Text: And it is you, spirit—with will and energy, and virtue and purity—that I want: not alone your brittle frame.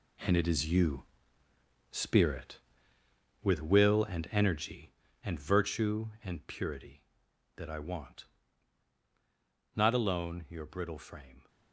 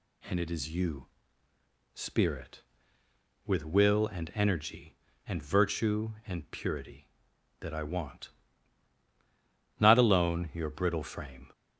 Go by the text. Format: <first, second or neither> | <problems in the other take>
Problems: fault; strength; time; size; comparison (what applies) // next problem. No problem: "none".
second | gets quieter; strong; throughout; 10 dB